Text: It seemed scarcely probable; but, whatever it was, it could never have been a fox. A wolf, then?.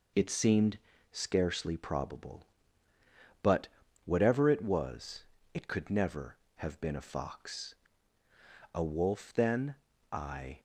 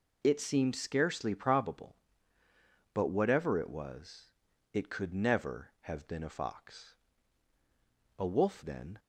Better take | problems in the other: second | pauses between "seemed" and "scarcely"; slight; at 0.7 s; 0.34 s long // goes on to say "I"; slight; from 10.1 s on; 0.48 s long

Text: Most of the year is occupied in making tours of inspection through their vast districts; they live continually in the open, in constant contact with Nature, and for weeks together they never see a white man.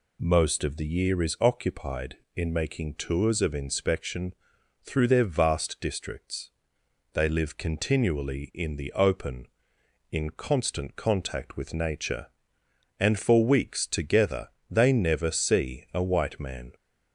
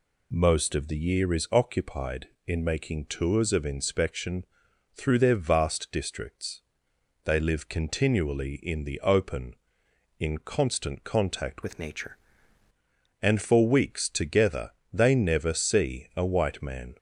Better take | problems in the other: first | pauses between "inspection" and "through"; noticeable; at 4.4 s; 0.50 s long; noticeable in the first // changes voice from "with" to "Nature"; from 11.6 to 12.1 s; 0.5 s long // pauses between "together" and "they"; slight; at 14.7 s; 0.22 s long; slight in the first

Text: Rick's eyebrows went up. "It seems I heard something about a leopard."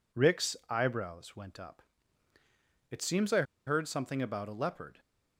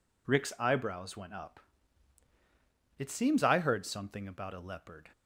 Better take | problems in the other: second | pauses between "I" and "heard"; slight; at 3.4 s; 0.24 s long

